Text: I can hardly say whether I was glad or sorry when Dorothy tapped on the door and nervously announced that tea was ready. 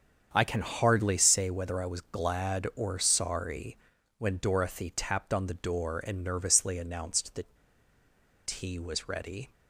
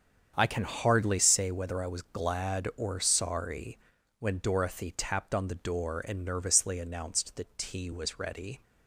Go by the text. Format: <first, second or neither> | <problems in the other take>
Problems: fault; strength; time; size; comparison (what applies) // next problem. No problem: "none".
second | starts louder than the rest; strong; until 1.3 s; 7.5 dB; strong in the second // pauses between "sorry" and "when"; at 3.7 s; 0.42 s long; also in the second // pauses between "that" and "tea"; noticeable; at 7.5 s; 0.90 s long